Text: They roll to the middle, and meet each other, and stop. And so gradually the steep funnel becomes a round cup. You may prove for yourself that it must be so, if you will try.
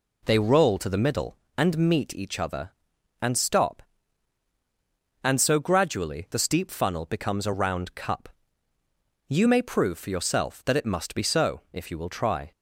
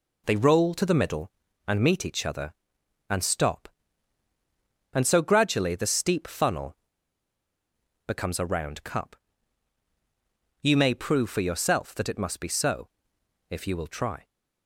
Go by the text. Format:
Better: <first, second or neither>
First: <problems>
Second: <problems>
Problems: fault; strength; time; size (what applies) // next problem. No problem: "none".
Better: first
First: none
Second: pauses between "funnel" and "becomes"; strong; at 6.7 s; 1.3 s long